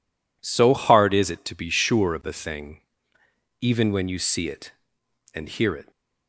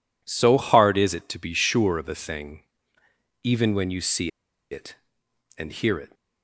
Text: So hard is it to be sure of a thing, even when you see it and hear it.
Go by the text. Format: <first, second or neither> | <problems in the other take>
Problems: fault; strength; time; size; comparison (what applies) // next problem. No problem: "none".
first | pauses between "see" and "it"; at 4.3 s; 0.41 s long